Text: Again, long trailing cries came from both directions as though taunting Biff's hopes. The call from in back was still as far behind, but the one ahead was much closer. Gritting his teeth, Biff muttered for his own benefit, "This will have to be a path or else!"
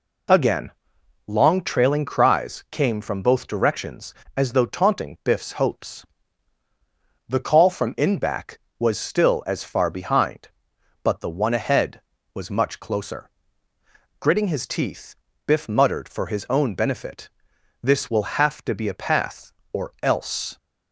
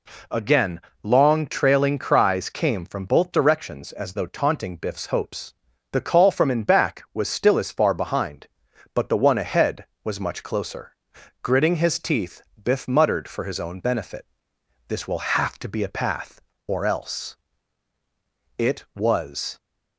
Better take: first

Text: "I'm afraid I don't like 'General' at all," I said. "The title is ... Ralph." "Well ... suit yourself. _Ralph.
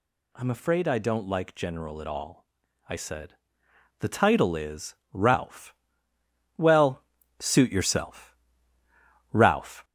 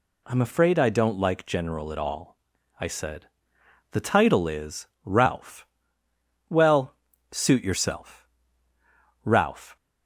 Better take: second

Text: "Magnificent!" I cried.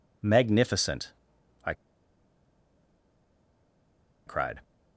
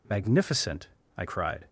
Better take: second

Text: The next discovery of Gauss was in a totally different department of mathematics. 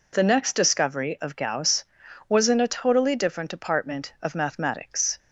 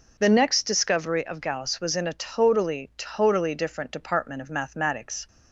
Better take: first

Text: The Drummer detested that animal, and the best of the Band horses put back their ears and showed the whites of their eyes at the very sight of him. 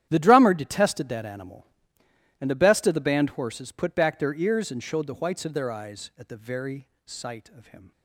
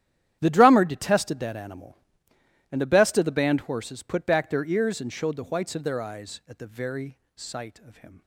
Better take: neither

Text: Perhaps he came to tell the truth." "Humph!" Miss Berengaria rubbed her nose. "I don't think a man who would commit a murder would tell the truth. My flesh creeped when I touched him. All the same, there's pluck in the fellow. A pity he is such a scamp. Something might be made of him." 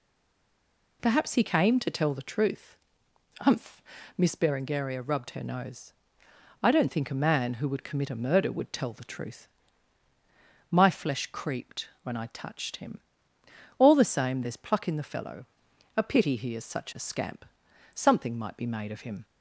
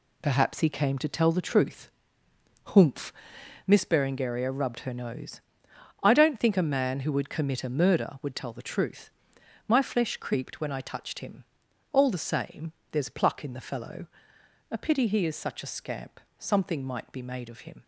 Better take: second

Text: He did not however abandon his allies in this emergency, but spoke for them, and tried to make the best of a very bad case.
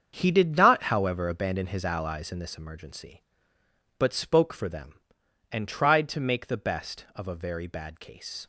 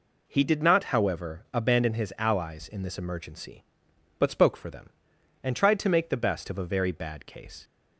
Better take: second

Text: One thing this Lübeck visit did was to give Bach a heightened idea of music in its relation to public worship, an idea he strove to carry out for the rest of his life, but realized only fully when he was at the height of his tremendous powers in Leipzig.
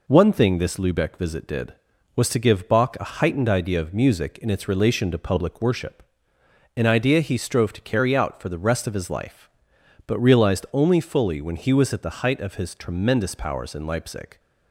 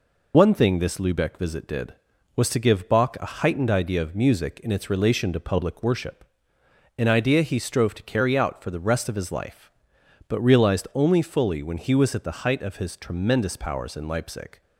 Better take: first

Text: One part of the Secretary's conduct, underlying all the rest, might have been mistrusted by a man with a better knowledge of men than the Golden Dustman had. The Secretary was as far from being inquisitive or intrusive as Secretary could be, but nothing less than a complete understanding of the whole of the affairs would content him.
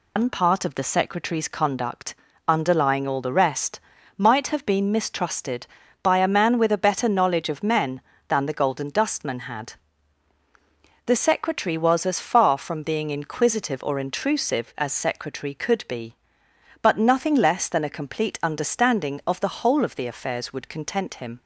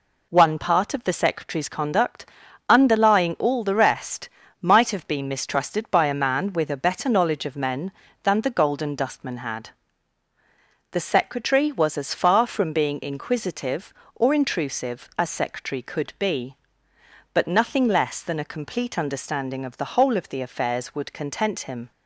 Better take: second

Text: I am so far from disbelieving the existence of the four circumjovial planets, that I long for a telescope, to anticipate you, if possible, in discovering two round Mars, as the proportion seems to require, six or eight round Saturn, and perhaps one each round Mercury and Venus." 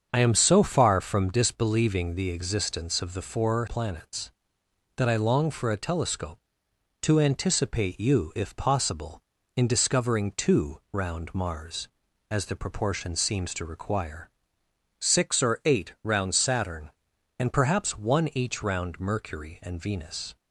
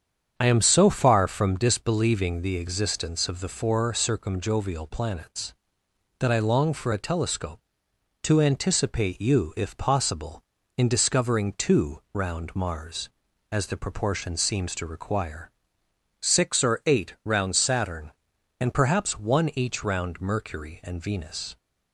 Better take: second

